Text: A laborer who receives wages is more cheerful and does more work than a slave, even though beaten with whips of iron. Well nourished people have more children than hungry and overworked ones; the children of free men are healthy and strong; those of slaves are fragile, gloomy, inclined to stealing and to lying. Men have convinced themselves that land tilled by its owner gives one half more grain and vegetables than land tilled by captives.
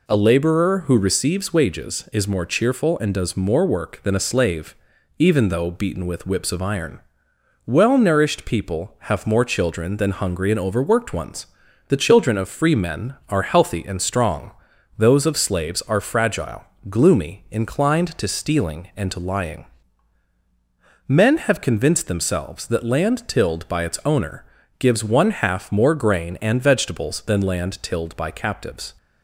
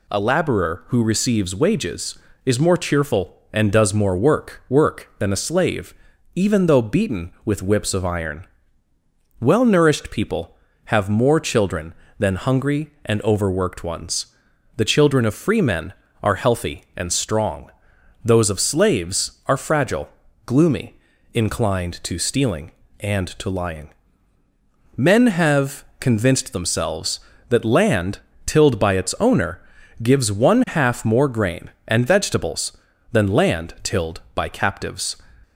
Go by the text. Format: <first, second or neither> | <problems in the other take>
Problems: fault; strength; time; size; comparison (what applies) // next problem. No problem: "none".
first | says "work" twice; at 4.6 s // pauses between "have" and "convinced"; slight; at 25.8 s; 0.16 s long // pauses between "land" and "tilled"; slight; at 28.1 s; 0.26 s long // pauses between "owner" and "gives"; at 29.6 s; 0.42 s long; slight in the first